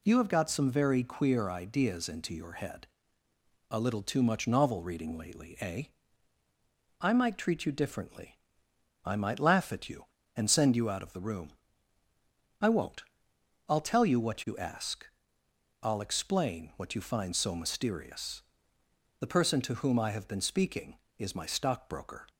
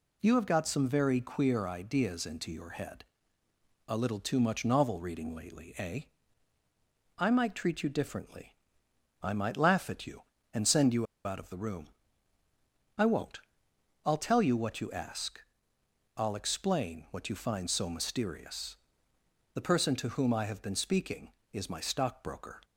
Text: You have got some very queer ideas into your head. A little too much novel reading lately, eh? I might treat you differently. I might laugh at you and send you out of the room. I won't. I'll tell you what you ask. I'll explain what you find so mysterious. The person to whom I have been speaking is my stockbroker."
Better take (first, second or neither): first